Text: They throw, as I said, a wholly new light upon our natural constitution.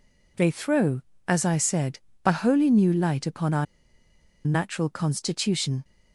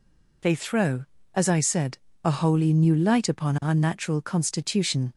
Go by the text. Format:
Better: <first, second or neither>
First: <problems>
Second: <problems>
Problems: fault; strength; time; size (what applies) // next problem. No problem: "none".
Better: second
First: pauses between "our" and "natural"; noticeable; at 3.6 s; 0.80 s long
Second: none